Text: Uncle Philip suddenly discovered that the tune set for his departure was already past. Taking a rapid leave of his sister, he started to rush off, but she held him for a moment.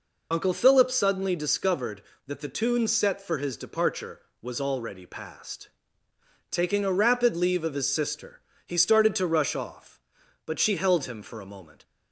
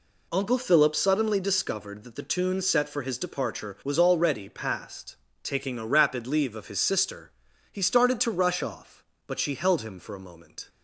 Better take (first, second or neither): second